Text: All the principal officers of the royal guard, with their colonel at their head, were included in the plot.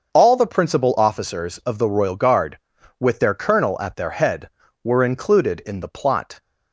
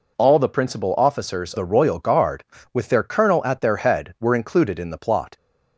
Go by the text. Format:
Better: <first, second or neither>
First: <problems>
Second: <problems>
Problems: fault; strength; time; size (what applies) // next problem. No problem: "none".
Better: first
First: none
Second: skips "of"; at 1.5 s